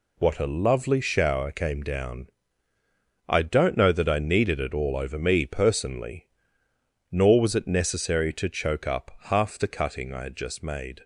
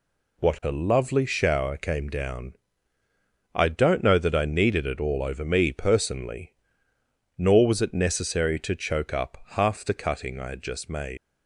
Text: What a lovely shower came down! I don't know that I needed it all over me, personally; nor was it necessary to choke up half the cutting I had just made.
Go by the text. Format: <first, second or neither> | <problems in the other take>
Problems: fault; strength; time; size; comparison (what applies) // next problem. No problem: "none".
first | leaves "made" unfinished; at 11.1 s; 125 ms